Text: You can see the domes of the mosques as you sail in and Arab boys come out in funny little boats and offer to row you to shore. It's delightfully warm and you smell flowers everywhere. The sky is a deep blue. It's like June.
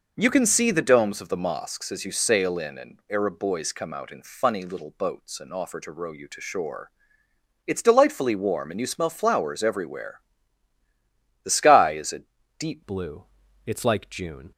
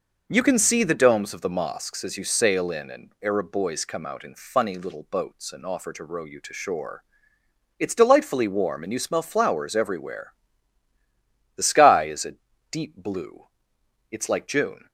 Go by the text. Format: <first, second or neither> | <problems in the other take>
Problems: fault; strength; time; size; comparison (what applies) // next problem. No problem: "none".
second | pauses between "a" and "deep"; at 12.2 s; 0.38 s long; also in the second // changes voice at "blue"; from 12.8 s on; 1.7 s long